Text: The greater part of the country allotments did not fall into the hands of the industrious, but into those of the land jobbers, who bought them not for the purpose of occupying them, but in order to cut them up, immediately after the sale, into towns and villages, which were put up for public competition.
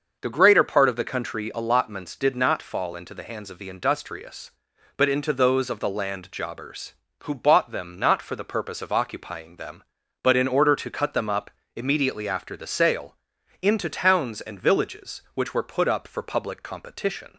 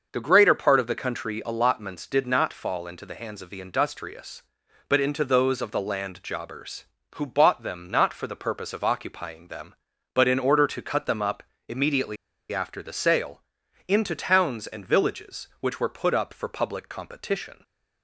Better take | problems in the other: first | starts louder than the rest; noticeable; until 1.1 s; 6 dB; noticeable in the first // pauses between "immediately" and "after"; at 12.1 s; 0.36 s long

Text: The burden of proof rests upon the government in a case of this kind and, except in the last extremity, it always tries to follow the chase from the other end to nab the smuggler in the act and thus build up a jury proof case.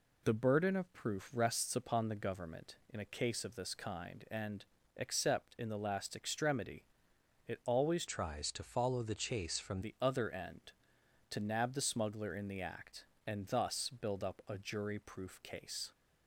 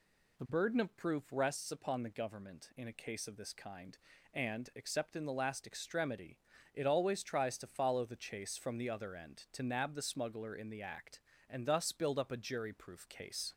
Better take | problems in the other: second | changes voice from "tries" to "from"; from 8.0 to 9.7 s; 1.7 s long

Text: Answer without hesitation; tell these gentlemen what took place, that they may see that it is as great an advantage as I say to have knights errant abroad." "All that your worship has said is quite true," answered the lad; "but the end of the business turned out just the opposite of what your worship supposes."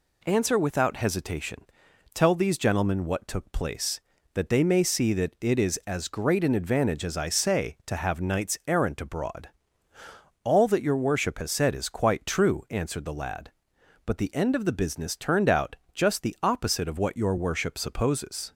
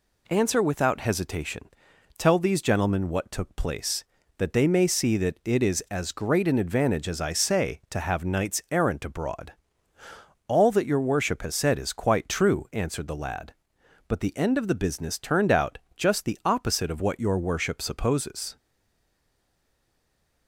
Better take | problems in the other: first | pauses between "out" and "just"; slight; at 15.7 s; 0.18 s long; slight in the first // stays silent after the last word; noticeable; from 18.5 s on; 1.9 s long

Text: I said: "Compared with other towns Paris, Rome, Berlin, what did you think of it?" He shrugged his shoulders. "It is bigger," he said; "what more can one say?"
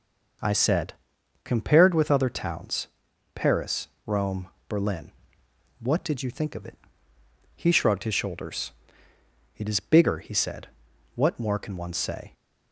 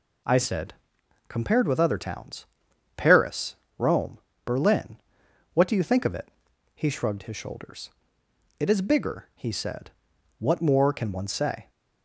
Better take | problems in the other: first | pauses between "towns" and "Paris"; noticeable; at 2.4 s; 0.50 s long; noticeable in the first // says "do" for "did"; at 5.6 s

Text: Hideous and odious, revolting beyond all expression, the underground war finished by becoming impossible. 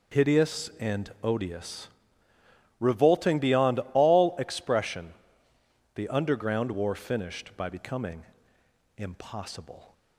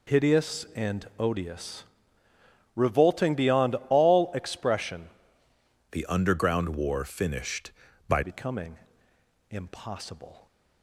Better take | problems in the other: first | changes voice from "the" to "by"; from 5.9 to 8.2 s; 2.3 s long // pauses between "becoming" and "impossible"; noticeable; at 8.7 s; 0.74 s long; noticeable in the first

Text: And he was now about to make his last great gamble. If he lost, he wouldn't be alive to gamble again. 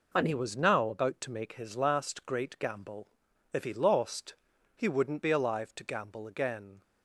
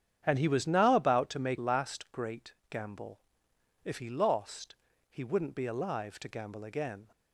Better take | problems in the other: first | starts louder than the rest; strong; until 1.2 s; 8.5 dB // skips "his"; at 1.5 s // pauses between "great" and "gamble"; slight; at 2.5 s; 0.18 s long

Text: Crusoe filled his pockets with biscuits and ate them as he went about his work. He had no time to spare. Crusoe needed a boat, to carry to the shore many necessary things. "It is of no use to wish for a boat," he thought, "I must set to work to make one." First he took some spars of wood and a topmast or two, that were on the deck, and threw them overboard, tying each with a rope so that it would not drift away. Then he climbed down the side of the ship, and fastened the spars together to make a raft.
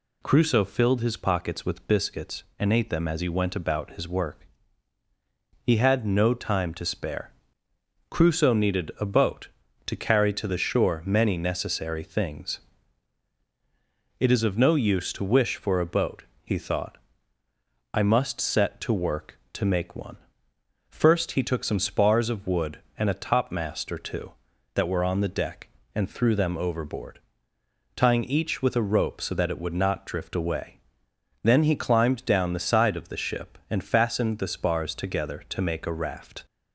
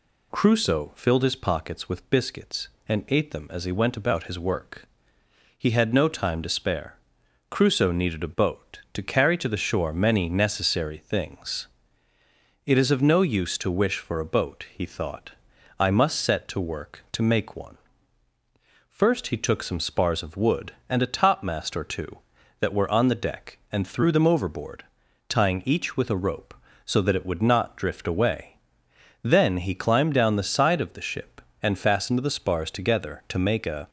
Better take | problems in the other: first | stops before "raft"; at 33.8 s

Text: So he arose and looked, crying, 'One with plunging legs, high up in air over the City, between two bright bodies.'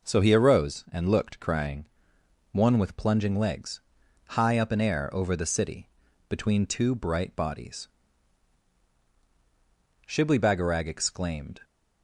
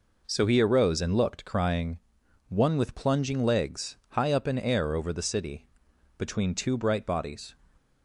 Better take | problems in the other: second | goes on to say "Shibli Bagarag exclaimed"; from 10.0 s on; 1.5 s long

